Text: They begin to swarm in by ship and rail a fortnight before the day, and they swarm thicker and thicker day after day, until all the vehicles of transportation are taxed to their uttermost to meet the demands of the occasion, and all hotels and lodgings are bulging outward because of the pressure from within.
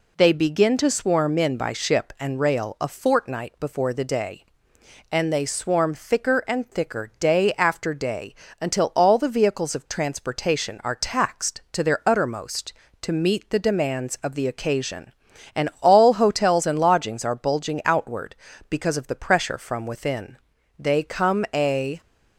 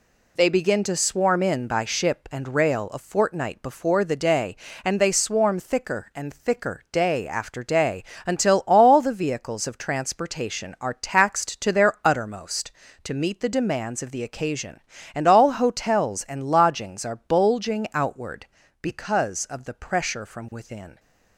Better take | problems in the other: second | goes on to say "They come a"; noticeable; from 20.7 s on; 1.2 s long

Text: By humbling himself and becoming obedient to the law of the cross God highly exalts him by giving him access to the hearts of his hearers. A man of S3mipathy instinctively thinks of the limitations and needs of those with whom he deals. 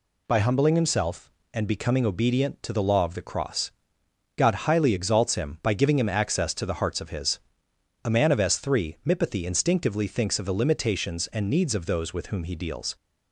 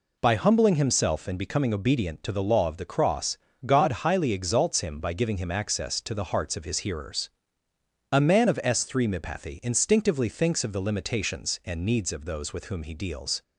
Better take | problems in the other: second | pauses between "cross" and "God"; noticeable; at 3.7 s; 0.66 s long; slight in the second // skips "hearers"; at 7.7 s

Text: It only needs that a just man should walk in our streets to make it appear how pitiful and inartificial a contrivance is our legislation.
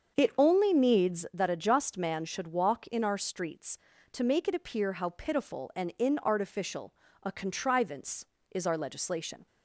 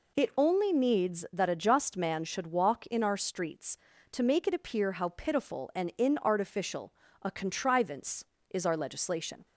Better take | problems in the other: second | starts louder than the rest; until 1.5 s; 7 dB // pauses between "inartificial" and "a"; slight; at 6.9 s; 0.32 s long; slight in the second

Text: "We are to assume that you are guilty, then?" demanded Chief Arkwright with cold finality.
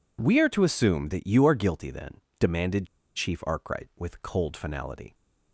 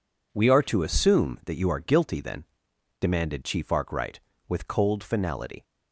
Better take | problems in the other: second | pauses between "demanded" and "Chief"; slight; at 2.8 s; 0.29 s long

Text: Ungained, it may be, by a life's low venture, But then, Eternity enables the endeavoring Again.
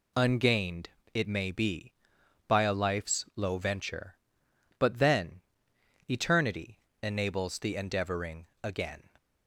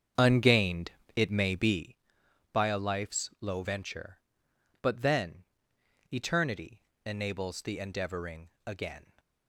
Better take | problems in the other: first | starts louder than the rest; strong; until 2.0 s; 7.5 dB // pauses between "Eternity" and "enables"; slight; at 6.8 s; 0.22 s long; slight in the first

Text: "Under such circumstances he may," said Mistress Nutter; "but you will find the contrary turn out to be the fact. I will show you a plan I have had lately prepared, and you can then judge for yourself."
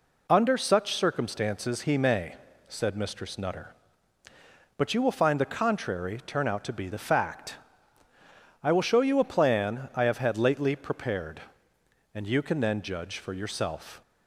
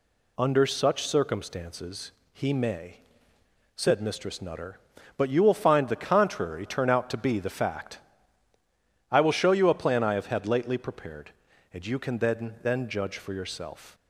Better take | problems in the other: first | pauses between "circumstances" and "he"; slight; at 2.1 s; 0.20 s long // says "then" twice; at 12.6 s

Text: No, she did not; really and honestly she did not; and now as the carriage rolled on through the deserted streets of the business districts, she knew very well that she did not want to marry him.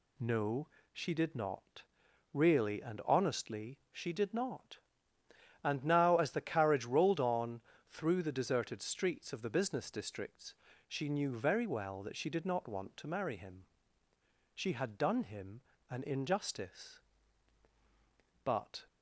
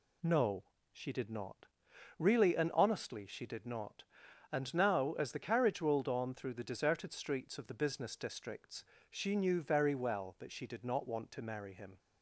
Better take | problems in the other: second | pauses between "on" and "through"; slight; at 7.6 s; 0.30 s long // goes on to say "She had done him an injustice but"; strong; from 14.5 s on; 4.3 s long

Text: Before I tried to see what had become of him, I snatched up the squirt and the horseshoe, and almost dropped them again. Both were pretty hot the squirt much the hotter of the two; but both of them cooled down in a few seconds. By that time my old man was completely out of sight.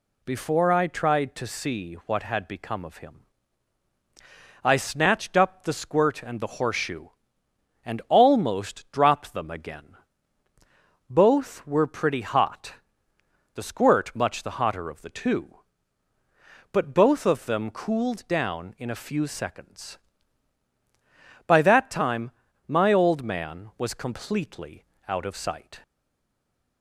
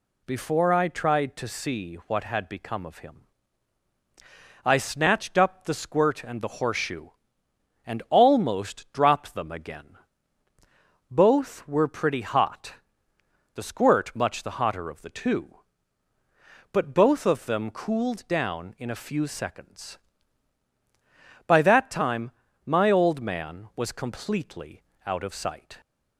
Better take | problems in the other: second | pauses between "hot" and "the"; noticeable; at 12.7 s; 0.80 s long; noticeable in the second // pauses between "time" and "my"; slight; at 22.3 s; 0.36 s long; slight in the second // pauses between "completely" and "out"; slight; at 24.8 s; 0.22 s long; slight in the second // stays silent after the last word; from 25.8 s on; 1.0 s long

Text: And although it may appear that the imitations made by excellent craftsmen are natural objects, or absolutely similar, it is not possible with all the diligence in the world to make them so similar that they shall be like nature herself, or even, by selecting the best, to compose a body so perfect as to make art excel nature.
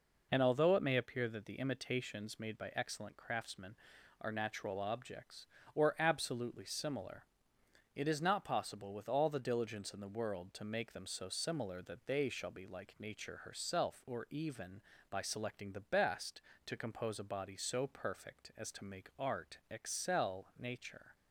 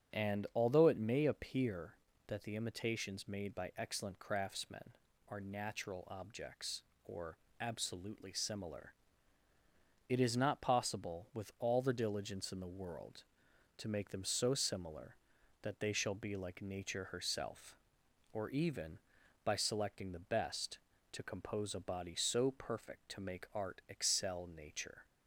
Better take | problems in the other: first | starts louder than the rest; strong; until 1.2 s; 8 dB // pauses between "or" and "absolutely"; slight; at 7.3 s; 0.24 s long // skips "as"; at 23.0 s

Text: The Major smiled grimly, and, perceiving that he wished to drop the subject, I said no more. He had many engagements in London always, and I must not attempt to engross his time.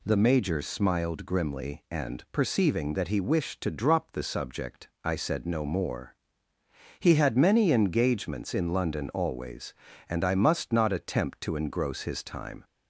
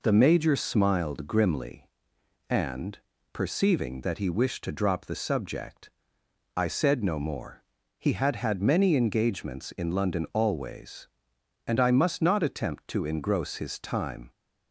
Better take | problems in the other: first | says "had" twice; at 8.3 s

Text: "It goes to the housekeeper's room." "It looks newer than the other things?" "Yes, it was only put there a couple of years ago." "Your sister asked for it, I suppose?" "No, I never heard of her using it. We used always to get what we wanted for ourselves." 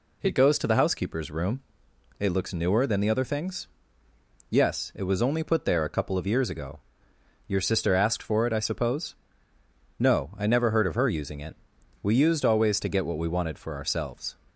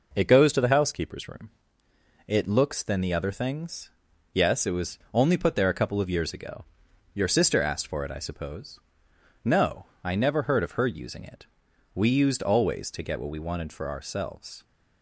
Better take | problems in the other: first | skips "newer"; at 2.8 s // pauses between "was" and "only"; slight; at 4.9 s; 0.16 s long

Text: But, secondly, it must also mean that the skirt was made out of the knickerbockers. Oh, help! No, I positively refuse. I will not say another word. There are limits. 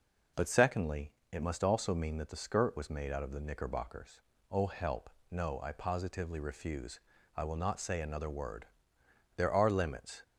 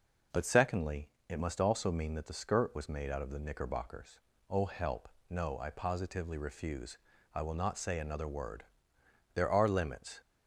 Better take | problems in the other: neither | none

